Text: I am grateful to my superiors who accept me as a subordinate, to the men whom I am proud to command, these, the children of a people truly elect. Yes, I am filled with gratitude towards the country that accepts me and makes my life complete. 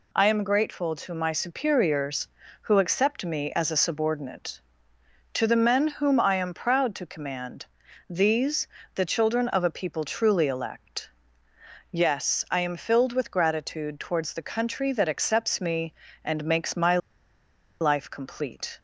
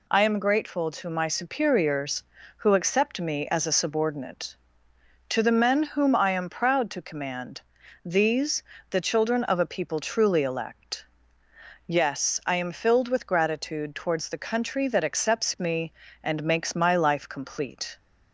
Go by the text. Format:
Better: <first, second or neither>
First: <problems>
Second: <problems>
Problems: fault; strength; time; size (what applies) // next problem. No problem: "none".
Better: second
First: pauses between "my" and "life"; noticeable; at 16.9 s; 0.83 s long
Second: none